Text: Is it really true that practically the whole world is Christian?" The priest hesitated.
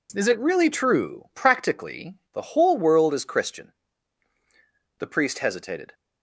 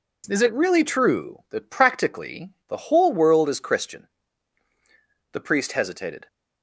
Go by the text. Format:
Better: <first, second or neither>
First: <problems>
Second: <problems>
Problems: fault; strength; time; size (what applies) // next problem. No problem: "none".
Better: second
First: skips "that"; at 1.3 s // pauses between "practically" and "the"; slight; at 2.1 s; 0.18 s long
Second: pauses between "practically" and "the"; slight; at 2.5 s; 0.18 s long